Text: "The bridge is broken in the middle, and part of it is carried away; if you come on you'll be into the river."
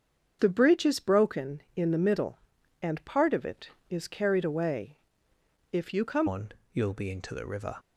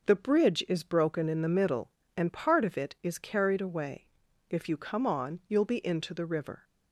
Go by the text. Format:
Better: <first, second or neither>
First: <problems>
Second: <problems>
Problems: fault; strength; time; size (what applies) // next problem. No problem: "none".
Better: second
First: starts louder than the rest; strong; until 1.4 s; 7 dB // changes voice at "on"; from 6.2 s on; 1.5 s long // pauses between "on" and "you'll"; slight; at 6.5 s; 0.22 s long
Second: none